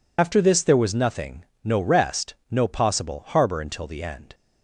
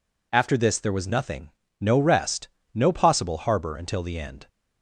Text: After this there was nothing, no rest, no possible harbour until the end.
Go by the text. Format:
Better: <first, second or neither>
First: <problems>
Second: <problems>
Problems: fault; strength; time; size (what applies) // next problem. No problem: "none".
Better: second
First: loses the start of "After"; at 0.1 s; 55 ms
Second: none